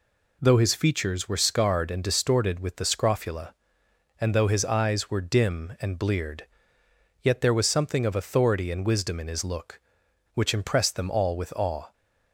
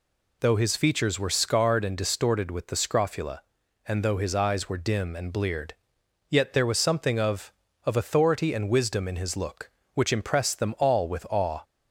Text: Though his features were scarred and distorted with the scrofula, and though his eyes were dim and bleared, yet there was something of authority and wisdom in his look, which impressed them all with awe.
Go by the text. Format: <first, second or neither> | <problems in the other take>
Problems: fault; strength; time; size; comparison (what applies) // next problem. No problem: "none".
first | says "of" twice; at 7.8 s